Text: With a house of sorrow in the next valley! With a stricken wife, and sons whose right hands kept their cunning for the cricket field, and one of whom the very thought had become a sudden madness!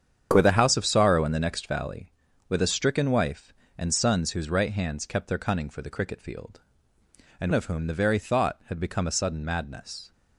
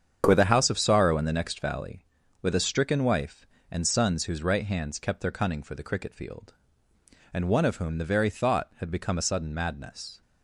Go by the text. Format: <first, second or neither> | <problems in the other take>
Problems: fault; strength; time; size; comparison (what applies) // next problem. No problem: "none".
second | starts louder than the rest; strong; until 1.3 s; 8.5 dB; strong in the second // skips "one"; at 7.5 s